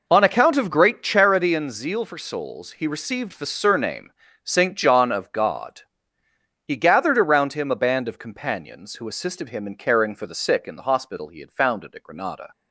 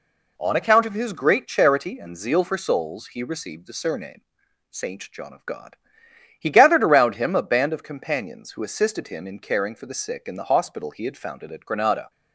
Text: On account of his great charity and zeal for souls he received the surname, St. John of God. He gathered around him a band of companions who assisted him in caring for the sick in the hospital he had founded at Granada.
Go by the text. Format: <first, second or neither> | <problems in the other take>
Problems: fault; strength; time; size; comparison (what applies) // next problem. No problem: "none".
second | skips "his"; at 0.7 s